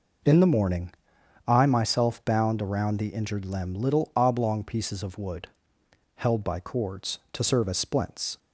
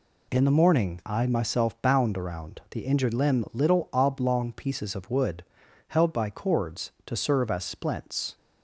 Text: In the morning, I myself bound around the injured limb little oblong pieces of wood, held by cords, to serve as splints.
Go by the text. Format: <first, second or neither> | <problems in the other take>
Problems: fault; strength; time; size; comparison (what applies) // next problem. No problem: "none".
neither | none